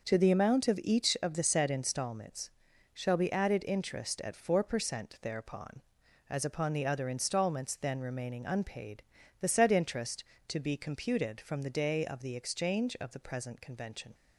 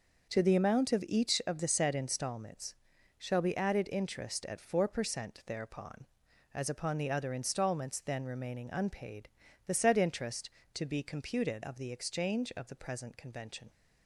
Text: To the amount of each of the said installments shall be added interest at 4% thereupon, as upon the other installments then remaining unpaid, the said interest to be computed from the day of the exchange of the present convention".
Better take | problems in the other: first | starts louder than the rest; noticeable; until 1.3 s; 6 dB; also in the first // pauses between "installments" and "shall"; at 2.7 s; 0.42 s long; also in the first // skips "from the day"; at 11.6 s

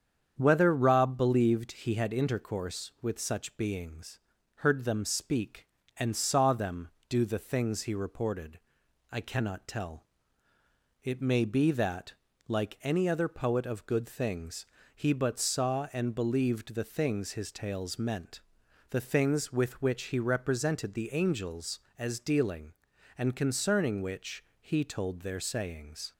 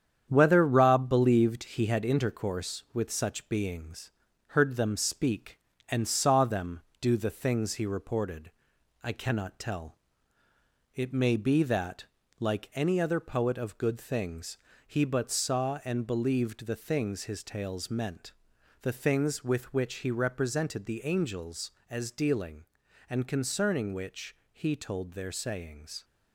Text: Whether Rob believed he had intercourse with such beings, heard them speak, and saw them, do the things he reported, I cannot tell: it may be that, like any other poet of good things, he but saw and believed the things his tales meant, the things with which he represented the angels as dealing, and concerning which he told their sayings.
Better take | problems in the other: first | gets quieter; noticeable; throughout; 6 dB // starts louder than the rest; strong; until 1.3 s; 8.5 dB; strong in the first // pauses between "which" and "he"; slight; at 24.3 s; 0.16 s long; slight in the first

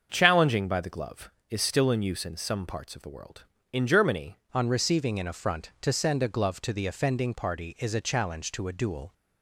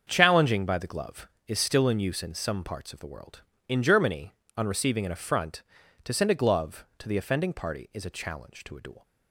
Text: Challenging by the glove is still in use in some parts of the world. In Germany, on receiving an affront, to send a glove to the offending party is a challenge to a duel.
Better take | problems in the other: second | starts louder than the rest; until 1.1 s; 6.5 dB; also in the second // changes voice at "on"; from 4.5 s on; 4.6 s long

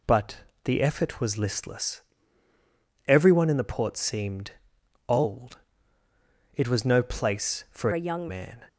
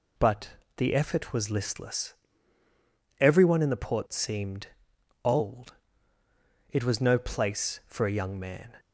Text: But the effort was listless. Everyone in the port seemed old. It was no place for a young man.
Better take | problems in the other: second | pauses between "But" and "the"; slight; at 0.3 s; 0.28 s long; slight in the second // pauses between "seemed" and "old"; noticeable; at 4.5 s; 0.56 s long; noticeable in the second // changes voice from "a" to "young"; from 7.9 to 8.2 s; 0.3 s long

